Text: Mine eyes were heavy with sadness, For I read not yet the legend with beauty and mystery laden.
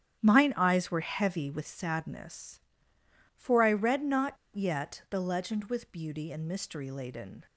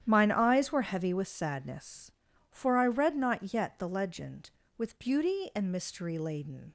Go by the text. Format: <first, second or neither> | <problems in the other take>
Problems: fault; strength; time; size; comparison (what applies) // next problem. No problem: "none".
second | starts louder than the rest; strong; until 1.2 s; 10 dB; strong in the second // pauses between "not" and "yet"; slight; at 4.3 s; 0.20 s long